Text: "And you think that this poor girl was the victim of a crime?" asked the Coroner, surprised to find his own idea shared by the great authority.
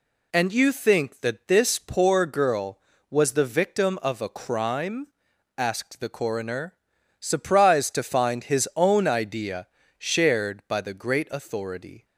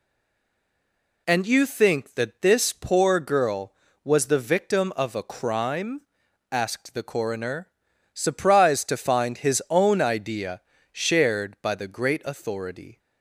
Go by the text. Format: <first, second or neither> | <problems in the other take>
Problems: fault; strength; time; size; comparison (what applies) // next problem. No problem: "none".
first | stays silent before the first word; noticeable; until 1.2 s; 1.2 s long // pauses between "idea" and "shared"; slight; at 10.6 s; 0.30 s long; slight in the first